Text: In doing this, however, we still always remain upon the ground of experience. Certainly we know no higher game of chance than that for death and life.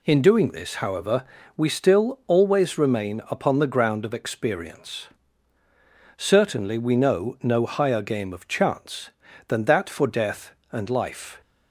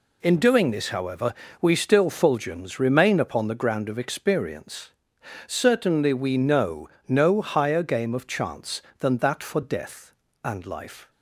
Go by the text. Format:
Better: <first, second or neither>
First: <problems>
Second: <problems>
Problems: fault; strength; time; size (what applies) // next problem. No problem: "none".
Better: first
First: none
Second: says "fulgens" for "always"; at 2.1 s // pauses between "know" and "no"; slight; at 6.8 s; 0.20 s long